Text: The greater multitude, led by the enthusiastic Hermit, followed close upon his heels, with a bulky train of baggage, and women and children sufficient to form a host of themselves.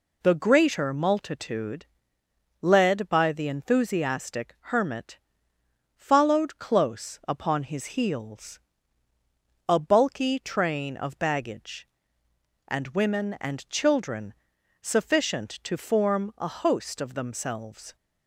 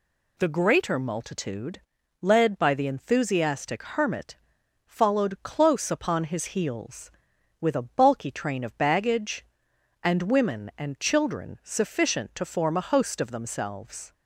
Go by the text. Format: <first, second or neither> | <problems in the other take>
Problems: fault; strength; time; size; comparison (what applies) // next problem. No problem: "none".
second | skips "with"; at 9.1 s // pauses between "children" and "sufficient"; noticeable; at 14.3 s; 0.48 s long